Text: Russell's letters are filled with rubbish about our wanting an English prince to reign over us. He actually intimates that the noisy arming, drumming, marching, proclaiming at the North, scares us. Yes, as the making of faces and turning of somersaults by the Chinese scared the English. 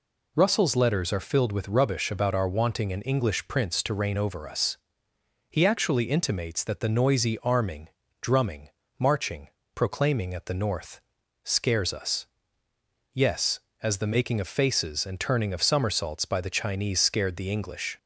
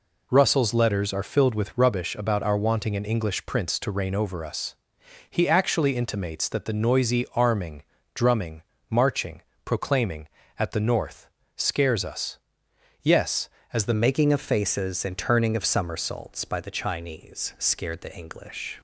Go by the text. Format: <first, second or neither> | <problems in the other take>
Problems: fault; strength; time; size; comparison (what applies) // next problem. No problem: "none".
first | changes voice at "making"; from 13.9 s on; 4.8 s long